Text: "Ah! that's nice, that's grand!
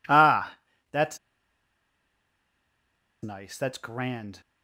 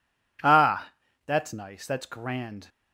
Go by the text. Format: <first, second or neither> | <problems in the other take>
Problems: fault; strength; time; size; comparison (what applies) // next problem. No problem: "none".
second | pauses between "that's" and "nice"; strong; at 1.1 s; 2.0 s long